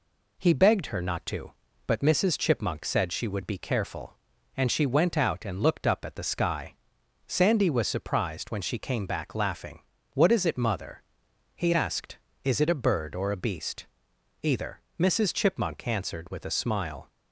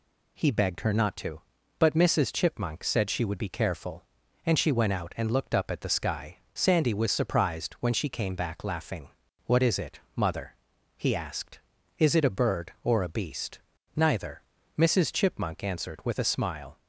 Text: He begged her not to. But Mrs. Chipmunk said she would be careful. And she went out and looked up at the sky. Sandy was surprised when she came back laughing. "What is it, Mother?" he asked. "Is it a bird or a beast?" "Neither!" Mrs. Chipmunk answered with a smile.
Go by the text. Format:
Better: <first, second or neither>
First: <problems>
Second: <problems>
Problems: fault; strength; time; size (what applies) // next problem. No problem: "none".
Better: second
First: says "Either" for "Neither"; at 14.4 s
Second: none